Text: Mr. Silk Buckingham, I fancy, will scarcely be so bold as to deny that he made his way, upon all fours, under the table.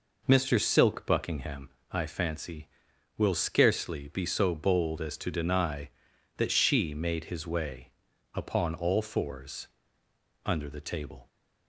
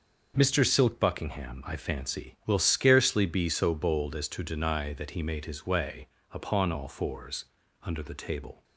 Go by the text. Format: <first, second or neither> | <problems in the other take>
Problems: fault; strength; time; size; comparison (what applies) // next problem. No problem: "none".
second | says "she" for "he"; at 6.5 s